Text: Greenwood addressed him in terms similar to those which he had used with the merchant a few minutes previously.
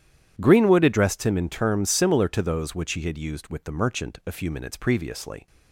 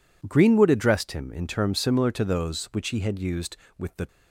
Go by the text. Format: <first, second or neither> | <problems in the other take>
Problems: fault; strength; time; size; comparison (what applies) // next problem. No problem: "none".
first | stops before "merchant a few minutes previously"; at 4.0 s